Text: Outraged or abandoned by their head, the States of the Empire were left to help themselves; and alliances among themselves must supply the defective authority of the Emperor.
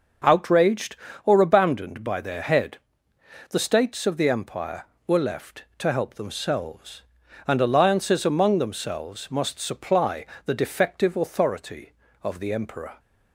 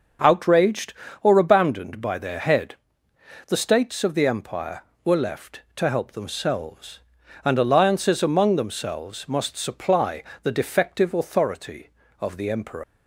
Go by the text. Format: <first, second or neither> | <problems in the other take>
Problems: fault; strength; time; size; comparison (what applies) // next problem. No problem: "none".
first | starts louder than the rest; until 1.5 s; 6.5 dB; also in the first // pauses between "supply" and "the"; slight; at 10.2 s; 0.20 s long; slight in the first // leaves "Emperor" unfinished; at 12.8 s; 125 ms